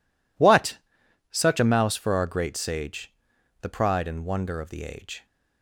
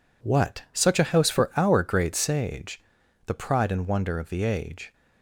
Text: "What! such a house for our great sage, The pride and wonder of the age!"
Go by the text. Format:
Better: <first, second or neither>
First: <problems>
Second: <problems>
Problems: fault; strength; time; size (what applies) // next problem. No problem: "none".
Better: second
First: says "mouse" for "house"; at 1.6 s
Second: none